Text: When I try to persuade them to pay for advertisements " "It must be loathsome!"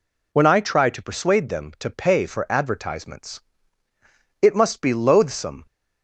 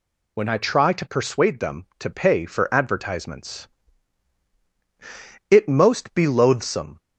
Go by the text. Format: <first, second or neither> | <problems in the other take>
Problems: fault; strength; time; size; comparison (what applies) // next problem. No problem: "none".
first | says "most" for "must"; at 5.6 s